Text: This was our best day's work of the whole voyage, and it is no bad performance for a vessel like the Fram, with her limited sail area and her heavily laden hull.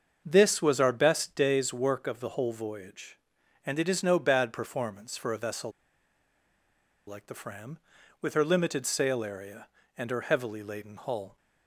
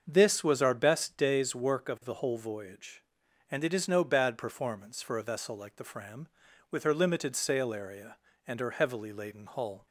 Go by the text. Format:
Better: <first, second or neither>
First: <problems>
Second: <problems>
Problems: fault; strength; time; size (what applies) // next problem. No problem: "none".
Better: second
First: starts louder than the rest; until 1.2 s; 6.5 dB // pauses between "vessel" and "like"; strong; at 5.7 s; 1.3 s long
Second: starts louder than the rest; until 1.0 s; 6.5 dB